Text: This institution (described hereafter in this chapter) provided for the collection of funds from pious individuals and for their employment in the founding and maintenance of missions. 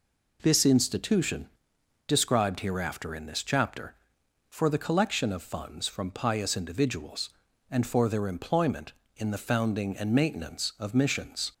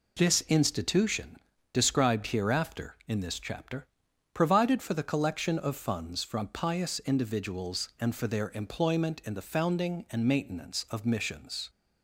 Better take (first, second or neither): second